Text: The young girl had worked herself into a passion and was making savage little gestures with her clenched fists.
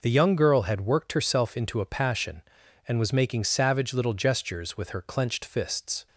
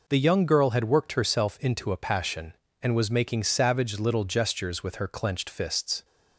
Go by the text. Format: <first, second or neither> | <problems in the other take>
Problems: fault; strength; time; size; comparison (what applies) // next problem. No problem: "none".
neither | none